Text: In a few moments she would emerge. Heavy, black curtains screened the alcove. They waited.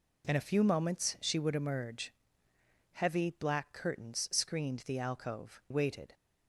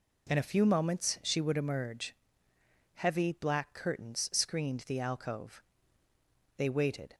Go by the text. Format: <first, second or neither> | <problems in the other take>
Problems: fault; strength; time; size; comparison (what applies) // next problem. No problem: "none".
second | skips "They"; at 5.6 s